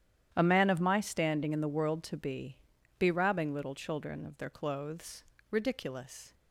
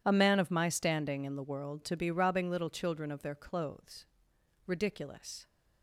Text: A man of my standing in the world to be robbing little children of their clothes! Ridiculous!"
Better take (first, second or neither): second